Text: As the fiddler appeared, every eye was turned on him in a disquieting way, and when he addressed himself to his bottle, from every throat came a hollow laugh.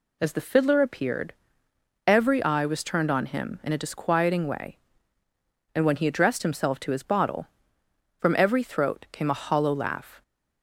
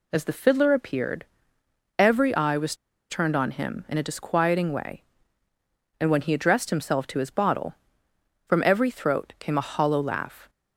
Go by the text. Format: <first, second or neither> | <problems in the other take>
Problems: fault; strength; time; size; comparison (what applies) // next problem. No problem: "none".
first | pauses between "was" and "turned"; slight; at 2.7 s; 0.35 s long